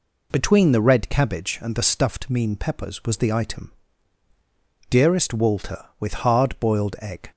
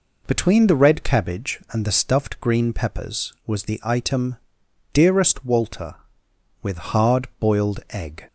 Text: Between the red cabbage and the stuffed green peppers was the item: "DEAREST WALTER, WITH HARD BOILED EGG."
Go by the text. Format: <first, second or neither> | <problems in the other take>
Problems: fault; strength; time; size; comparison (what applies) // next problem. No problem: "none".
second | says "mean" for "green"; at 2.2 s